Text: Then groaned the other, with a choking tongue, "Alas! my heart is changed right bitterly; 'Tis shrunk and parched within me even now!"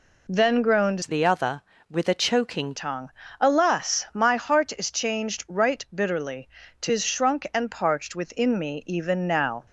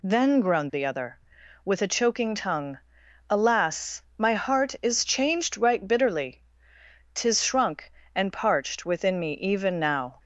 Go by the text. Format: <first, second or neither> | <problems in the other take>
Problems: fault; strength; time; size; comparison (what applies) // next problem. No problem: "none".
second | changes voice from "the" to "choking"; from 1.0 to 2.7 s; 1.7 s long